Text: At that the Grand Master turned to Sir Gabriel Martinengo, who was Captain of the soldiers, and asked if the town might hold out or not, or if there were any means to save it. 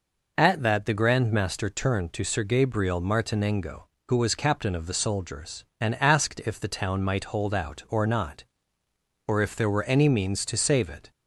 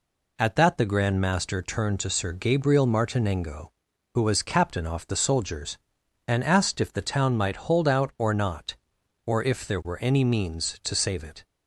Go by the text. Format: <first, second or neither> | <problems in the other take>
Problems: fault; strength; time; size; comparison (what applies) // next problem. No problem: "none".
first | says "off" for "of"; at 4.8 s